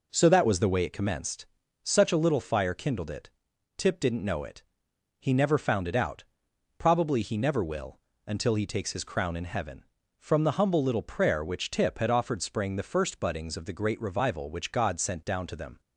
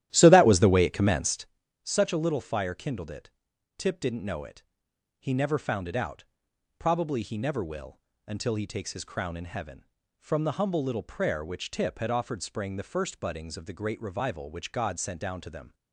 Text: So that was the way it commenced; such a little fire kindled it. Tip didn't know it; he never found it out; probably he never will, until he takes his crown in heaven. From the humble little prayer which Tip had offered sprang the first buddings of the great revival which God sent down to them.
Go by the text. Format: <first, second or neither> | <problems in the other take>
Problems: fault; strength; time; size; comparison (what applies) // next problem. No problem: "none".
first | starts louder than the rest; strong; until 1.5 s; 12.5 dB